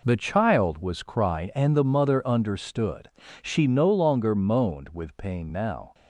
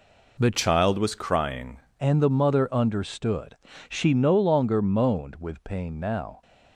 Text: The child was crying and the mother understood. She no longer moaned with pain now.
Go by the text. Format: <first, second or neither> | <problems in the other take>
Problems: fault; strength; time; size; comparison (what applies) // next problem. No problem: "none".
first | changes voice from "child" to "crying"; from 0.5 to 1.7 s; 1.2 s long